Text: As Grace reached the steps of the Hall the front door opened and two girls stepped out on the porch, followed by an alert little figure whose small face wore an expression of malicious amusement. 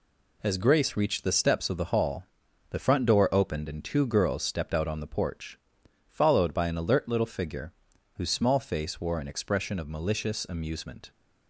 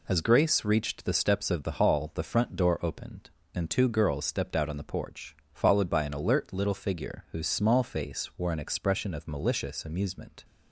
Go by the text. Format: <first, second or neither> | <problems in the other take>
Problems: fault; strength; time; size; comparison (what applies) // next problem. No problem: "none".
second | gets quieter; throughout; 7 dB // pauses between "Hall" and "the"; noticeable; at 2.2 s; 0.46 s long // pauses between "figure" and "whose"; at 7.7 s; 0.42 s long